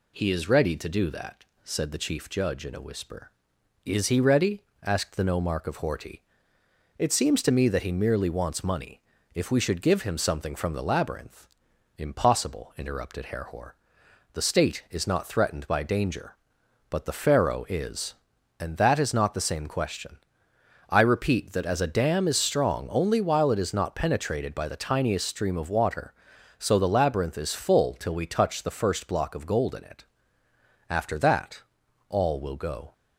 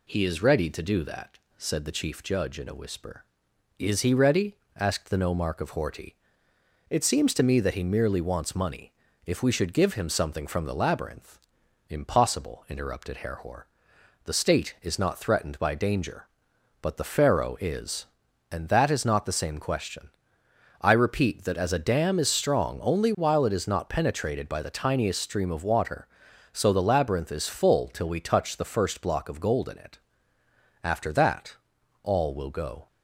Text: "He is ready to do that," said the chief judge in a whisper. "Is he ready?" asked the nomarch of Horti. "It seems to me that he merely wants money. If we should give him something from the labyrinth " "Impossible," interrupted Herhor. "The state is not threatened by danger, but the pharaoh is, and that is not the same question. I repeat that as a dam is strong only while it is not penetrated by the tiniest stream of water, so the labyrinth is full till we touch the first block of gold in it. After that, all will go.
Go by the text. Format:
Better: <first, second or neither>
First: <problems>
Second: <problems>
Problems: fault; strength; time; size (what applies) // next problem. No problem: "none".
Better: neither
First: none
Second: none